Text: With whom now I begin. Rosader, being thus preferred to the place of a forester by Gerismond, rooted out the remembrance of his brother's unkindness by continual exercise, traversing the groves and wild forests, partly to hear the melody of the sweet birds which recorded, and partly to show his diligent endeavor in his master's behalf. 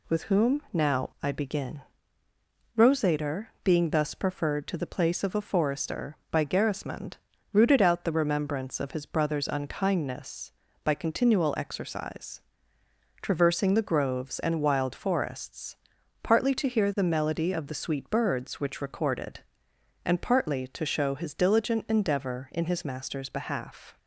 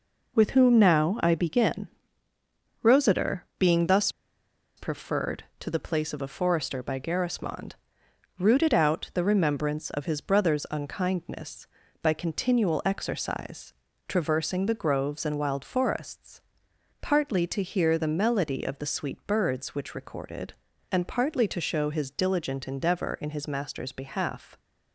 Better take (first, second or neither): first